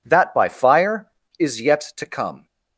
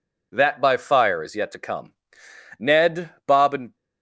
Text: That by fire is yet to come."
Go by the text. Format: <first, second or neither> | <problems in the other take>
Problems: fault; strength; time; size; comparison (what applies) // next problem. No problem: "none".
first | goes on to say "Ned Bob and"; noticeable; from 2.5 s on; 1.1 s long